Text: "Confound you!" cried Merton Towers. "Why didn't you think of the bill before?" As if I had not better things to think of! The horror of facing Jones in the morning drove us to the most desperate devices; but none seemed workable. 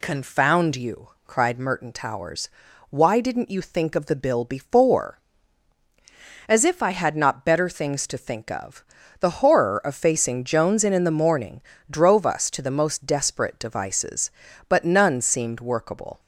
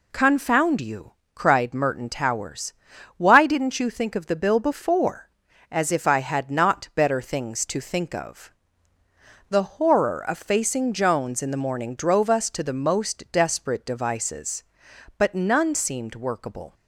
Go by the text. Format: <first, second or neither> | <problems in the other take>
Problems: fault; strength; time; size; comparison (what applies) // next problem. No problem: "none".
second | says "in" twice; at 10.9 s // pauses between "morning" and "drove"; slight; at 11.6 s; 0.26 s long